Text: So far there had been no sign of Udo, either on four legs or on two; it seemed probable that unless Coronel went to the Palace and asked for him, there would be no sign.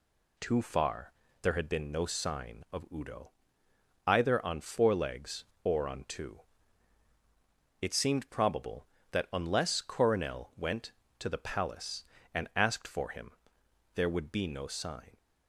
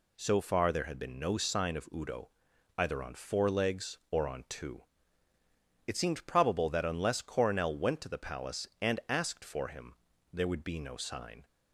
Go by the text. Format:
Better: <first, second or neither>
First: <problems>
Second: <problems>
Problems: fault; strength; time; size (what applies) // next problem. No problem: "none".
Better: second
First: says "Too" for "So"; at 0.3 s // pauses between "far" and "there"; slight; at 1.1 s; 0.28 s long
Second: none